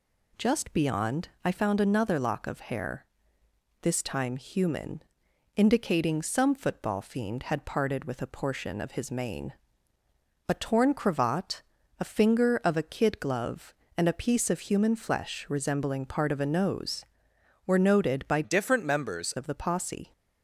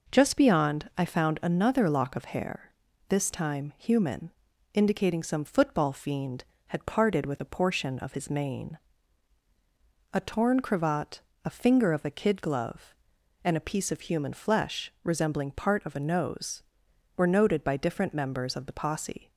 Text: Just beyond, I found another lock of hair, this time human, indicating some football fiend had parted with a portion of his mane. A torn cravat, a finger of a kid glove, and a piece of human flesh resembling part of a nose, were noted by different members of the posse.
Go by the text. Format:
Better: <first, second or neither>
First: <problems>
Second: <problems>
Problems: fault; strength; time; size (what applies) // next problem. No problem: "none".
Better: second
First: changes voice from "different" to "members"; from 18.4 to 19.3 s; 0.9 s long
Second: none